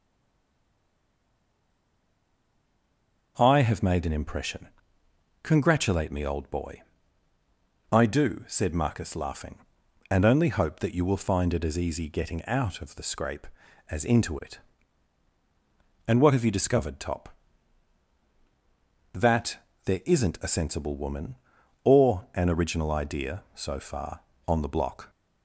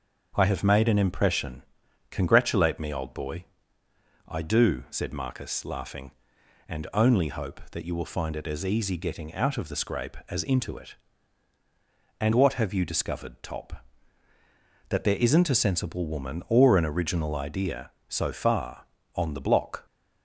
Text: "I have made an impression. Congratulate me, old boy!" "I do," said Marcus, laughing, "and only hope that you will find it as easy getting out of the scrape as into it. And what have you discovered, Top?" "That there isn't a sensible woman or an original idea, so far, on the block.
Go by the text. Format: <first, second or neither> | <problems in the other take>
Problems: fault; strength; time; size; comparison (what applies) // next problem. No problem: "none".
second | stays silent before the first word; strong; until 3.3 s; 3.3 s long // starts louder than the rest; noticeable; until 4.3 s; 6 dB; also in the second // pauses between "That" and "there"; slight; at 19.5 s; 0.26 s long